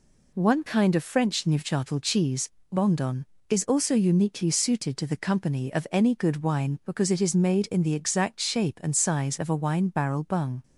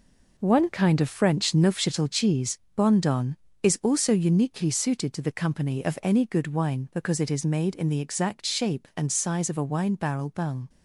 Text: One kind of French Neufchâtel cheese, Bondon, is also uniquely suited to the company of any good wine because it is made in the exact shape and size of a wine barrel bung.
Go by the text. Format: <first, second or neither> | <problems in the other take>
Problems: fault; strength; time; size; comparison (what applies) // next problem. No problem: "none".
first | gets quieter; strong; throughout; 8 dB